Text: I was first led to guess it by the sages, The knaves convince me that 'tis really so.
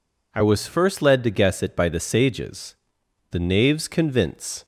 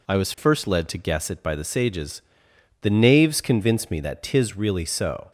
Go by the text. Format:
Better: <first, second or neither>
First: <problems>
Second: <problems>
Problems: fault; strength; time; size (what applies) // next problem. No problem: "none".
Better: second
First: stops before "me that tis really so"; at 4.6 s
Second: none